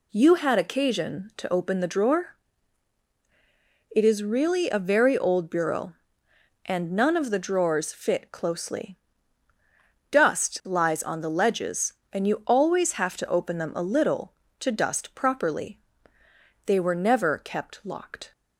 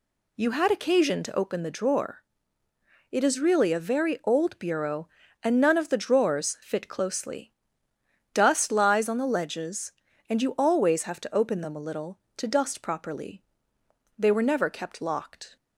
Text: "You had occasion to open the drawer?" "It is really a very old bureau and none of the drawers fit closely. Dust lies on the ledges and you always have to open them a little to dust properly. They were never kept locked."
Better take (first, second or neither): neither